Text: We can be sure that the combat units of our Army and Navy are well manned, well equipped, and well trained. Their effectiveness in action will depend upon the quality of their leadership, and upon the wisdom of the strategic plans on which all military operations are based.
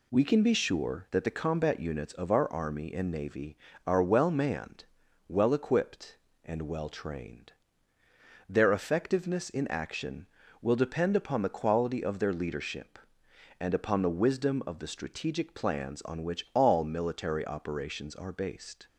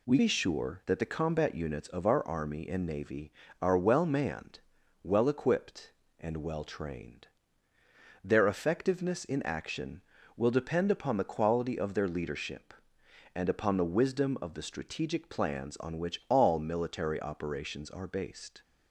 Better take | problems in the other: first | skips "can"; at 0.1 s

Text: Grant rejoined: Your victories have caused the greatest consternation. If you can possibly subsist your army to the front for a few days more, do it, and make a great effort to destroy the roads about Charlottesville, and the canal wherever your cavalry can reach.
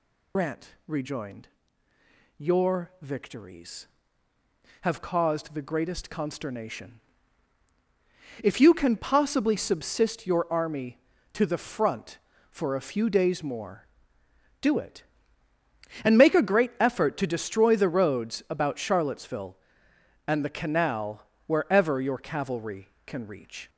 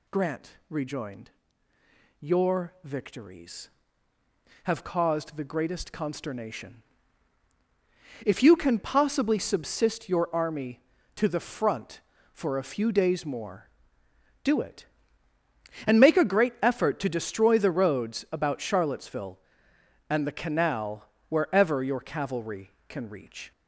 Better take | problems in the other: second | loses the start of "Grant"; at 0.3 s; 80 ms // pauses between "Grant" and "rejoined"; slight; at 0.6 s; 0.18 s long; slight in the second // pauses between "canal" and "wherever"; slight; at 21.2 s; 0.22 s long; slight in the second

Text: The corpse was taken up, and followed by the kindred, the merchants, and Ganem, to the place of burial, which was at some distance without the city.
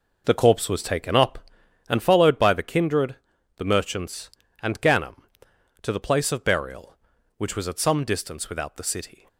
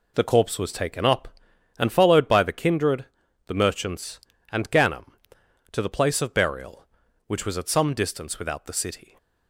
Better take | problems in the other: second | starts louder than the rest; noticeable; until 2.0 s; 5 dB

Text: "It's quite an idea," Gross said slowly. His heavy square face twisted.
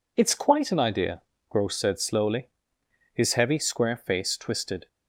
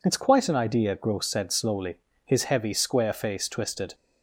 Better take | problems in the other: neither | none

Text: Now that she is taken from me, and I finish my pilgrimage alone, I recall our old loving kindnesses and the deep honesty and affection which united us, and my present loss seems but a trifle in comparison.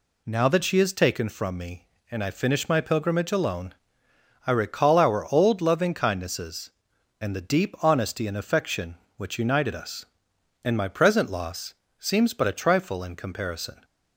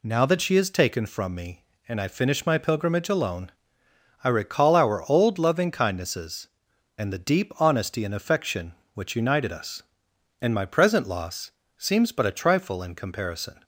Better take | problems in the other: neither | pauses between "loss" and "seems"; slight; the same in both

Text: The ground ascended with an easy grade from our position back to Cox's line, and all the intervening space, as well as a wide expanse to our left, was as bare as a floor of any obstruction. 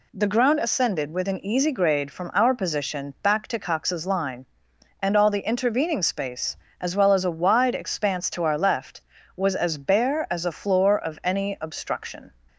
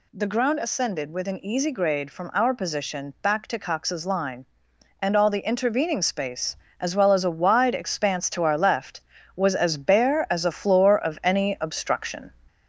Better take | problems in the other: first | gets louder; slight; throughout; 2.5 dB

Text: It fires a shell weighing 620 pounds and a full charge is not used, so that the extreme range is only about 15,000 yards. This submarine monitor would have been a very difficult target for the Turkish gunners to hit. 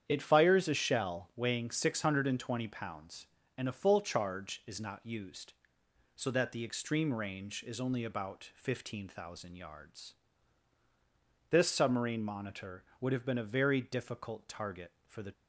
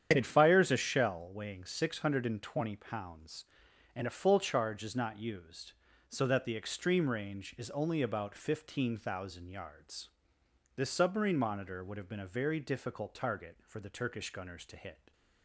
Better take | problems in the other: second | starts louder than the rest; strong; until 1.0 s; 9 dB; strong in the second // stops before "Turkish gunners to hit"; at 15.3 s

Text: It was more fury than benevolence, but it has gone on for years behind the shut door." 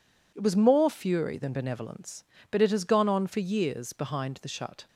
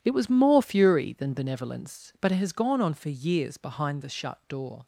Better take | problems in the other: second | stops before "door"; at 4.8 s

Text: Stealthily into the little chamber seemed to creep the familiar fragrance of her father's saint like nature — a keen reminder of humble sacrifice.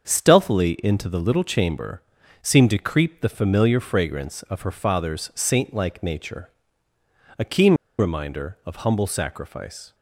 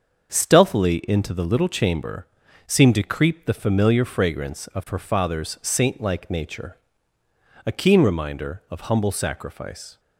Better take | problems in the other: second | starts louder than the rest; until 1.1 s; 7 dB; also in the second // pauses between "chamber" and "seemed"; at 1.9 s; 0.40 s long; also in the second // pauses between "keen" and "reminder"; slight; at 7.7 s; 0.24 s long

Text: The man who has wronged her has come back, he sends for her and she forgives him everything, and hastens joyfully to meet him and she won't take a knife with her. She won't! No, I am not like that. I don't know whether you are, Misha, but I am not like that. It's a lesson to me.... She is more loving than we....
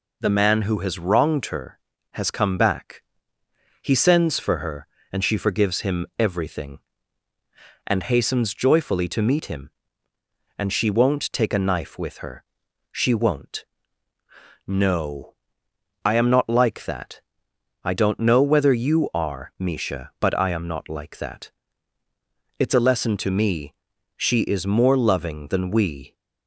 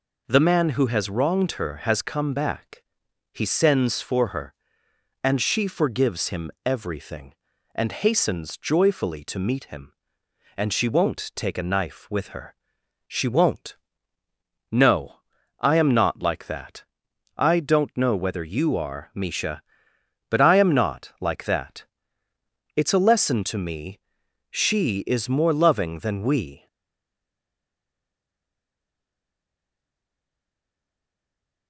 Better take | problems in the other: first | stays silent after the last word; strong; from 26.6 s on; 5.0 s long

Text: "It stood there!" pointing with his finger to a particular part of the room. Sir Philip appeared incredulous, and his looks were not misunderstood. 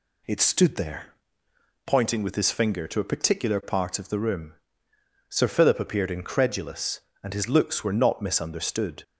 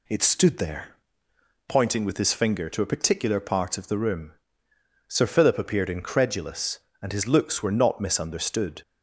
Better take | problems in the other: neither | none

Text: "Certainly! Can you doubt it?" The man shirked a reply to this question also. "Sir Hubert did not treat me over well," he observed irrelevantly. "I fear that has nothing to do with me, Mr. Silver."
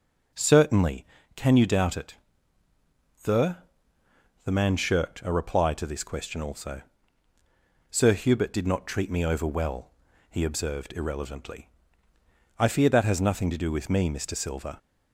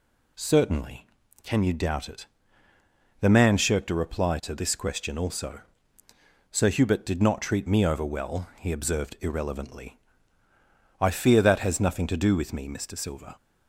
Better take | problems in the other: second | says "The" twice; at 4.4 s

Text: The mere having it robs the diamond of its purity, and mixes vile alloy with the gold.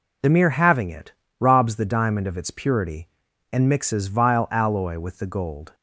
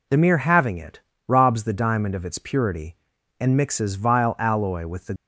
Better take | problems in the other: first | pauses between "it" and "robs"; slight; at 1.0 s; 0.28 s long; slight in the first // stops before "gold"; at 5.1 s

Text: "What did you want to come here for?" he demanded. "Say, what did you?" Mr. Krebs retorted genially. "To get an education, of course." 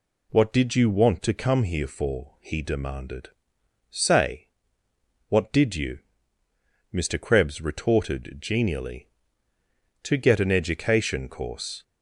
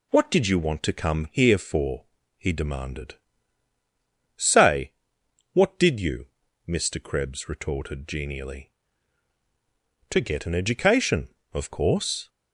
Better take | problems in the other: second | skips "of"; at 11.2 s

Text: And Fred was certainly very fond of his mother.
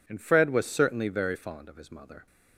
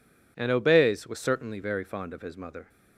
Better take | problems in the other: first | says "Obeys" for "Fred"; at 0.5 s

